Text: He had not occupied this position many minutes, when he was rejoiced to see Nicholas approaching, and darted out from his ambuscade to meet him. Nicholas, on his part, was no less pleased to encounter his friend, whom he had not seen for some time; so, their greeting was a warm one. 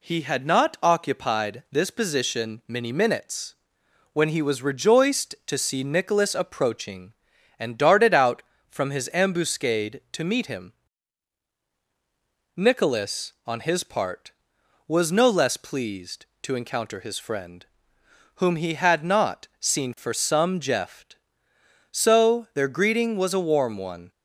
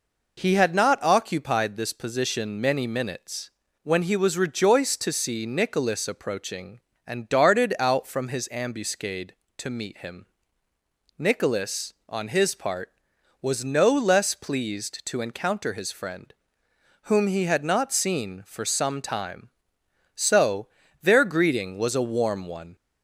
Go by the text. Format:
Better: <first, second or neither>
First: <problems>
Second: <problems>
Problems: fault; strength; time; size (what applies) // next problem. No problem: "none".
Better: second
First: says "jeft" for "time"; at 20.6 s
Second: none